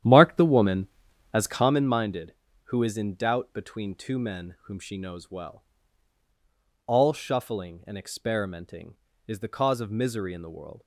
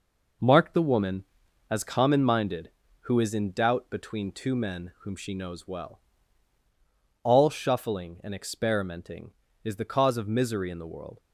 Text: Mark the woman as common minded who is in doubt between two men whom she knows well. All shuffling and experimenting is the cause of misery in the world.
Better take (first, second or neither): second